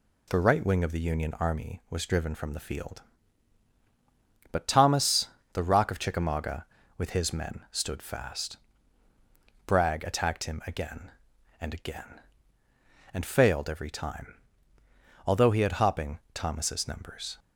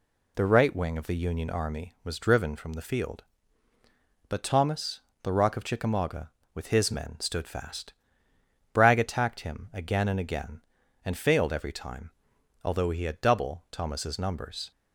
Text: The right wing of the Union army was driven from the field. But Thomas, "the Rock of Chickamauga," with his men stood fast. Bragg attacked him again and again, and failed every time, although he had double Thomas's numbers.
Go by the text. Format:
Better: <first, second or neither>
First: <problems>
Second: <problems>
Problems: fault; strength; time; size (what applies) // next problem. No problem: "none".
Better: second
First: says "hopping" for "double"; at 15.7 s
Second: none